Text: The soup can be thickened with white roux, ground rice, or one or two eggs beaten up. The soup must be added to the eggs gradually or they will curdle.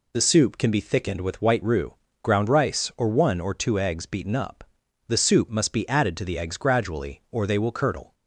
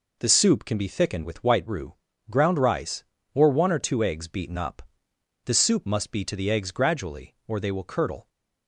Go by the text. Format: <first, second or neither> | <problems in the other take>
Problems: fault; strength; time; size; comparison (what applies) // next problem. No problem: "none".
first | skips "added"; at 6.2 s